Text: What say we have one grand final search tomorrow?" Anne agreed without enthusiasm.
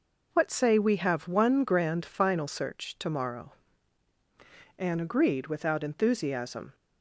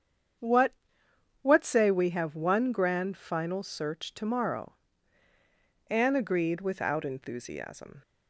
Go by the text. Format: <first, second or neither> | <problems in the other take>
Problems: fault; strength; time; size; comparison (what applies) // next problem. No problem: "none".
first | starts louder than the rest; strong; until 2.0 s; 8 dB // says "What" twice; at 1.4 s